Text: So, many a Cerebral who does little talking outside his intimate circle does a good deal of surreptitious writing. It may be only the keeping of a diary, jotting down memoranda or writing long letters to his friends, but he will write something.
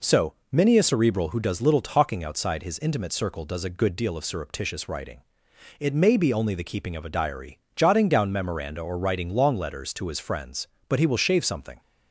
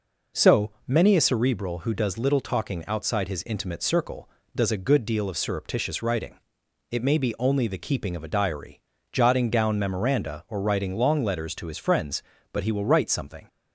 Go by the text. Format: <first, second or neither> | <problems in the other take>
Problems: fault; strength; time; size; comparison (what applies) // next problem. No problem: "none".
second | says "shave" for "write"; at 11.1 s